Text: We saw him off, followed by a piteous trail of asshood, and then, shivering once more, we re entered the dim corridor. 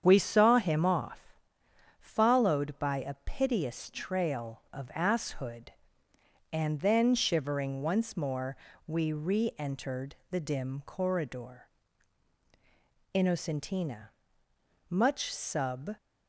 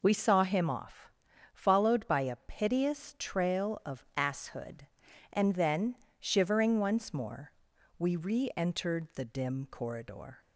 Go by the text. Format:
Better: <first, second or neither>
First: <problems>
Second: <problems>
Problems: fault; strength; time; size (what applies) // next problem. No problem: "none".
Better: second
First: starts louder than the rest; strong; until 1.0 s; 8 dB // pauses between "entered" and "the"; slight; at 10.1 s; 0.16 s long // goes on to say "Innocentina much sub"; strong; from 13.1 s on; 2.8 s long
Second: none